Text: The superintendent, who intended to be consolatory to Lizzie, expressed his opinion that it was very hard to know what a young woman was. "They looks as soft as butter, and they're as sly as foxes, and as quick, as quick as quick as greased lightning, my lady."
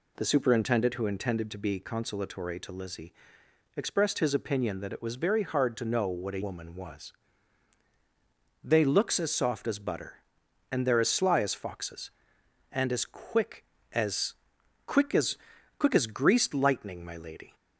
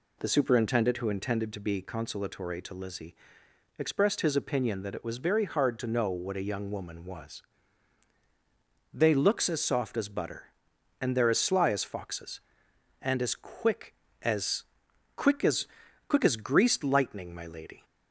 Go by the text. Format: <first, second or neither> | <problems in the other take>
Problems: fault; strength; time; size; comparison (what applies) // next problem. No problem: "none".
second | skips "young"; at 6.4 s // pauses between "as" and "quick"; noticeable; at 14.3 s; 0.50 s long; noticeable in the second // pauses between "as" and "quick"; at 15.3 s; 0.40 s long; also in the second